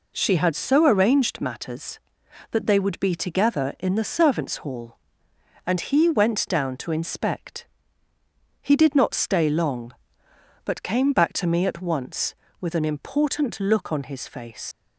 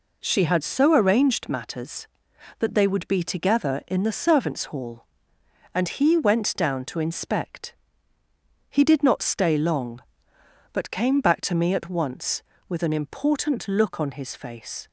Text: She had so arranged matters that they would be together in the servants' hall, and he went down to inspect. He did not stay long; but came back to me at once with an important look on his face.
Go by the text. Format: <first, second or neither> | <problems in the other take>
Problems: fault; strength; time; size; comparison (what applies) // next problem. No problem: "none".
second | leaves "face" unfinished; at 14.7 s; 80 ms